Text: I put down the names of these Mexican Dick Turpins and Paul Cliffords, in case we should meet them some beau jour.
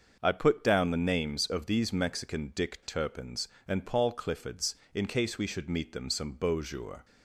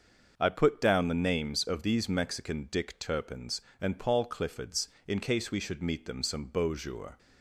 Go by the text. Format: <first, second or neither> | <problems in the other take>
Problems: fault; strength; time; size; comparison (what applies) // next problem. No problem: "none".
neither | starts louder than the rest; the same in both